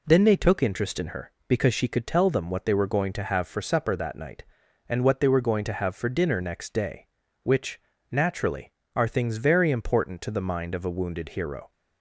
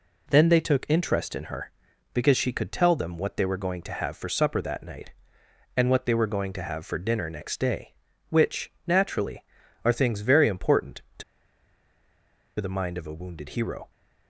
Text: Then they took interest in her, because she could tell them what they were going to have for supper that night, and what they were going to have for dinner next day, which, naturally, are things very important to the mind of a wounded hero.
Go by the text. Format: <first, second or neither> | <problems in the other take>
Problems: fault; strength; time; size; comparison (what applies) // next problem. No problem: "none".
first | pauses between "to" and "the"; strong; at 11.2 s; 1.3 s long